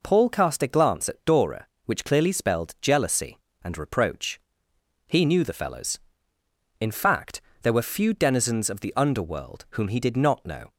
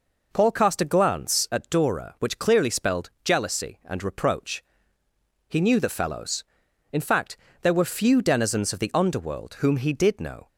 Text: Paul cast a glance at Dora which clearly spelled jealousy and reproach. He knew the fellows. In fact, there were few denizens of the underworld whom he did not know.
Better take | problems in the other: first | skips "not"; at 10.1 s

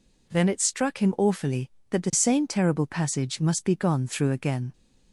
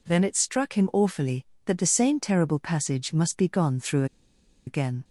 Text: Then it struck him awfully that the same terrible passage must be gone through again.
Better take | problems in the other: first | pauses between "through" and "again"; noticeable; at 4.0 s; 0.61 s long

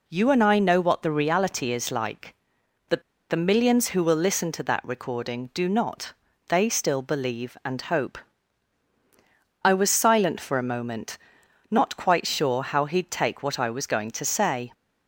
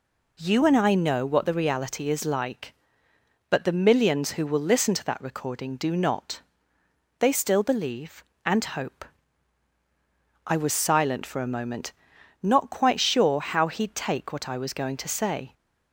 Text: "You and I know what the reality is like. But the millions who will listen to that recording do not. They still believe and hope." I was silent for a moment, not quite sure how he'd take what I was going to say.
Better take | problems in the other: second | pauses between "But" and "the"; slight; at 3.0 s; 0.27 s long

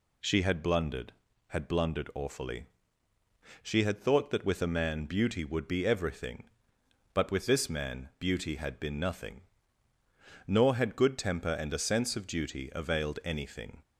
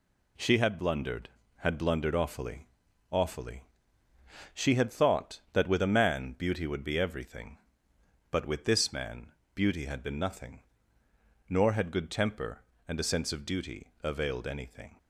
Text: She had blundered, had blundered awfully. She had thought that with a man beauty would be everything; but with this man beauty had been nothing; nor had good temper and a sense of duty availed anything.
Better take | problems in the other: first | says "awfully" twice; at 3.0 s // pauses between "man" and "beauty"; slight; at 9.3 s; 0.22 s long

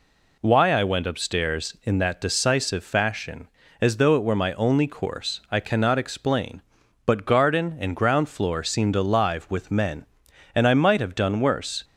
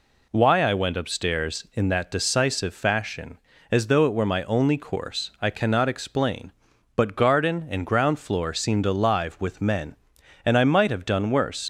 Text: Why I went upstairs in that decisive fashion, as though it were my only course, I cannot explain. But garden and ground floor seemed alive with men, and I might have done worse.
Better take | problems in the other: first | leaves "worse" unfinished; at 11.6 s; 60 ms

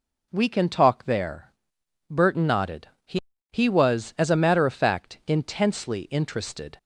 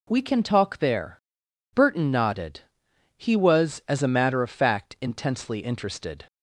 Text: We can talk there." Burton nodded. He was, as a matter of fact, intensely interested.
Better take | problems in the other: second | says "He" twice; at 3.5 s

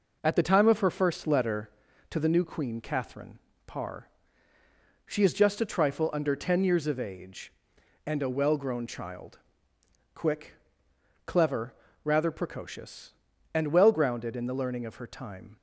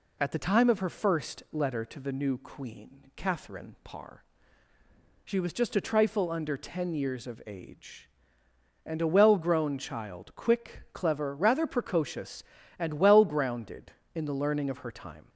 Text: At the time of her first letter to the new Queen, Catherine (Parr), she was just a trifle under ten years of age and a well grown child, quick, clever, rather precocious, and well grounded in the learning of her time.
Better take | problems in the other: second | says "is" for "was"; at 5.2 s

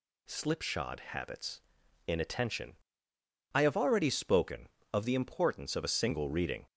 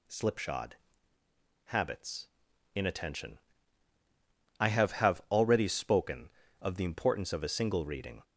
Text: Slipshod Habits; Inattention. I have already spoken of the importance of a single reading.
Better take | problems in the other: first | pauses between "Slipshod" and "Habits"; noticeable; at 0.7 s; 0.90 s long // says "have" twice; at 4.9 s

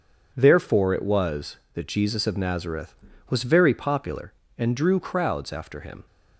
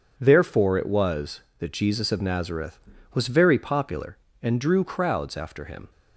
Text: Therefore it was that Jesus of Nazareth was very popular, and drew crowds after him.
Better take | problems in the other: neither | none

